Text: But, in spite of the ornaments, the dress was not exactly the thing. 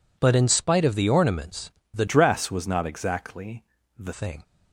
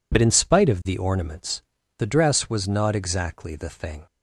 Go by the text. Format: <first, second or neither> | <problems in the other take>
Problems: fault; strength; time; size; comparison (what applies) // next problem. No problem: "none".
second | changes voice from "dress" to "the"; from 2.0 to 4.1 s; 2.1 s long // pauses between "exactly" and "the"; slight; at 3.6 s; 0.34 s long